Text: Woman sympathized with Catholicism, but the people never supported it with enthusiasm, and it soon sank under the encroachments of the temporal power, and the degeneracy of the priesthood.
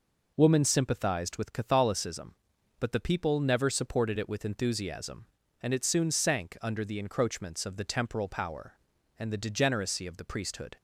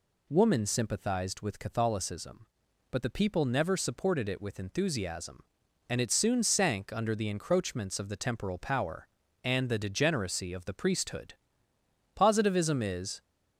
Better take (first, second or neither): first